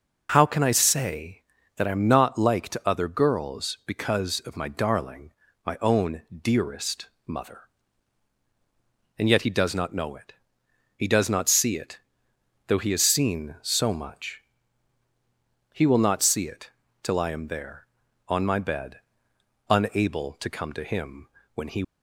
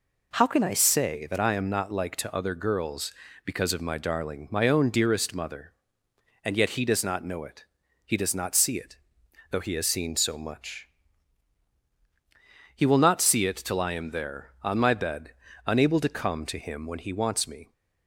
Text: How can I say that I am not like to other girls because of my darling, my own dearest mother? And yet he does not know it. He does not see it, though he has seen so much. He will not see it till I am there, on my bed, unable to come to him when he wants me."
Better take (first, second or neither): second